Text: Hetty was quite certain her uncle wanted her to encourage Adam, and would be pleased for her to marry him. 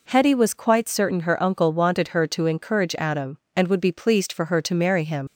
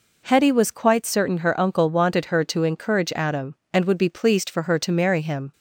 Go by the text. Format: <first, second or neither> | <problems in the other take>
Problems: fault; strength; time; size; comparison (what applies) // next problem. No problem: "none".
second | leaves "him" unfinished; at 5.2 s; 75 ms